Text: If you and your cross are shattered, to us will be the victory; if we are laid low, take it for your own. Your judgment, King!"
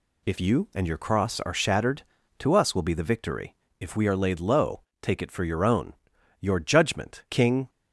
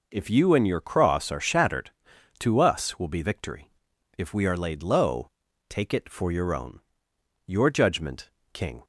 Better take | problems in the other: first | skips "the"; at 3.2 s

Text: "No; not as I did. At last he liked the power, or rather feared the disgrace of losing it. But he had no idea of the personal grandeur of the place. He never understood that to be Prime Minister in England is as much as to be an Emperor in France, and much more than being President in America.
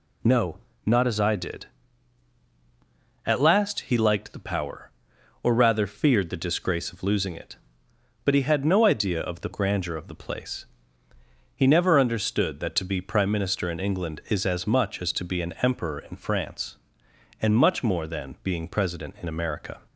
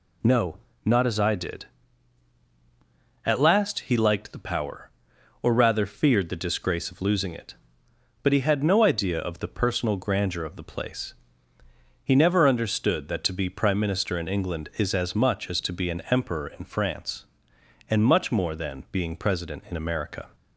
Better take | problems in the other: second | skips "personal"; at 9.5 s

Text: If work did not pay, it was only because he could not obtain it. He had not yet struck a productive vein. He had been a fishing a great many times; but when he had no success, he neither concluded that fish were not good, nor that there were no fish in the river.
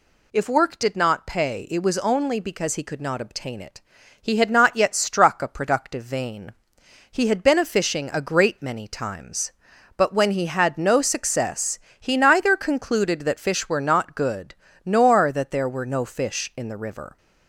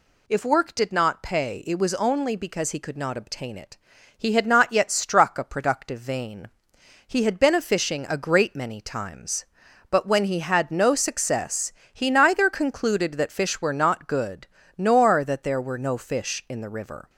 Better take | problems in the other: neither | none

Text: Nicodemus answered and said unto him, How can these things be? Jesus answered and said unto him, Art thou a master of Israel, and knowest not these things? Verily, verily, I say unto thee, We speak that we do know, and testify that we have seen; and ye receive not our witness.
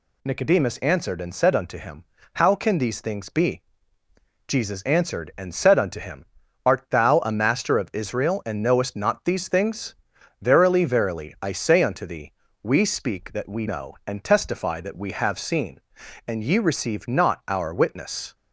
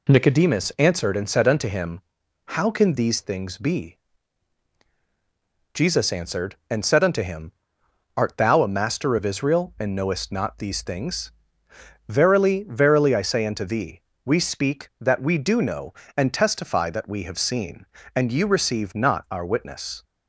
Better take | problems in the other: second | skips "do"; at 13.6 s

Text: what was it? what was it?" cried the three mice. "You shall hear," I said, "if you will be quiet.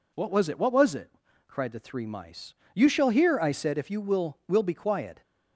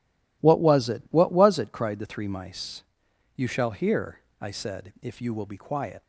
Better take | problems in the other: second | says "will" twice; at 4.4 s

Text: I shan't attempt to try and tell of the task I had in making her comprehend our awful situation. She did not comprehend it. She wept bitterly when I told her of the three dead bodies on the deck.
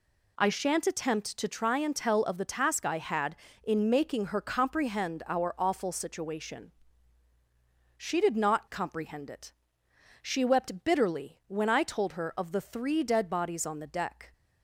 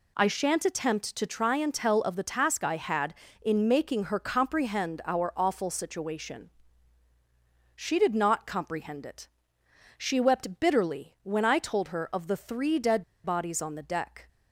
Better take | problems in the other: first | pauses between "dead" and "bodies"; slight; at 13.0 s; 0.22 s long

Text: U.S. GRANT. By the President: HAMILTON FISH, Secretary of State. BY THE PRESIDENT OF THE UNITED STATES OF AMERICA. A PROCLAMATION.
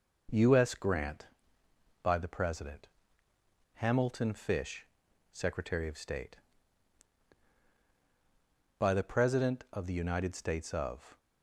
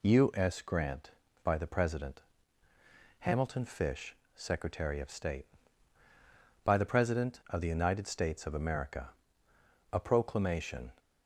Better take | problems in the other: second | stops before "AMERICA A PROCLAMATION"; at 11.1 s

